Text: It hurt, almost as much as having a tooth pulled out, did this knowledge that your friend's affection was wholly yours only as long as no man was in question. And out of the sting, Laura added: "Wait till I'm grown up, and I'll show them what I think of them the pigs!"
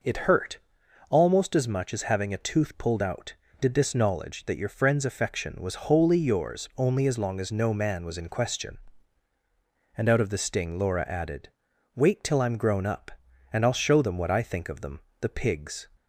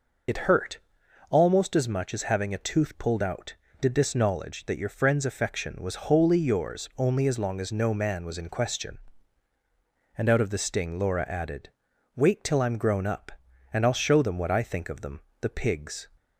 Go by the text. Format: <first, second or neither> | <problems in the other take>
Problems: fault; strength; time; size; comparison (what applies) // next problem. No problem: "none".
first | loses the start of "It"; at 0.2 s; 50 ms // pauses between "them" and "the"; slight; at 15.2 s; 0.18 s long; slight in the first